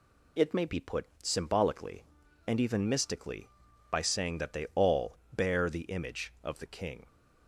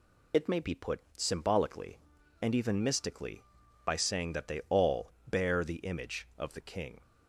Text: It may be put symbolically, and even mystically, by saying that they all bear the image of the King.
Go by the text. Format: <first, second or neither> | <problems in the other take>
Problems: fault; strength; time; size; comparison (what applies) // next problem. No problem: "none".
first | loses the start of "It"; at 0.3 s; 40 ms // pauses between "put" and "symbolically"; slight; at 1.0 s; 0.16 s long; slight in the first // pauses between "all" and "bear"; slight; at 5.1 s; 0.18 s long; slight in the first